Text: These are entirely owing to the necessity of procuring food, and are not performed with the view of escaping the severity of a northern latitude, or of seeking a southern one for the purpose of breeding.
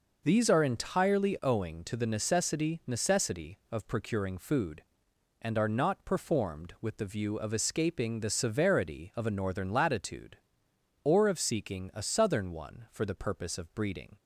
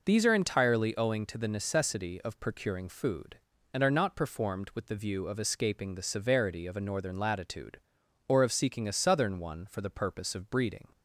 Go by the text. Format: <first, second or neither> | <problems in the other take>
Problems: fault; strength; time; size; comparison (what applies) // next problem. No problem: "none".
second | says "necessity" twice; at 2.8 s